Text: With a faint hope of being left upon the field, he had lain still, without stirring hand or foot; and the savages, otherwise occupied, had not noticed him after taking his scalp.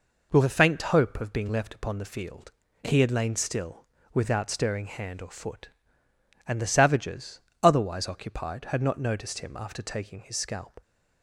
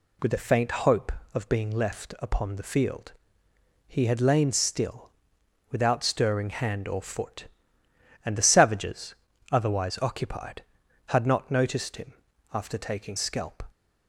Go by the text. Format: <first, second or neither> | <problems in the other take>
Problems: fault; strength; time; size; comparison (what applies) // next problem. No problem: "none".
first | pauses between "him" and "after"; at 12.1 s; 0.38 s long // skips "his"; at 13.1 s